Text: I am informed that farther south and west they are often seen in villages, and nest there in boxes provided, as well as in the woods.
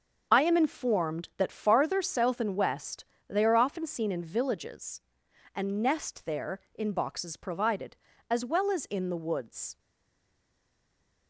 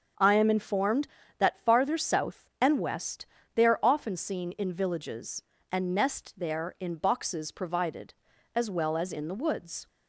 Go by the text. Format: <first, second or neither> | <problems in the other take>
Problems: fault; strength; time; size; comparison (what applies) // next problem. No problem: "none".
second | starts louder than the rest; noticeable; until 1.3 s; 6 dB; strong in the second // pauses between "west" and "they"; slight; at 3.0 s; 0.24 s long; slight in the second // stays silent after the last word; noticeable; from 9.7 s on; 1.5 s long